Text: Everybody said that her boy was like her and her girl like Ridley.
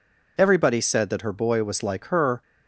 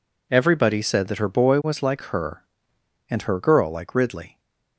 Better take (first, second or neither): second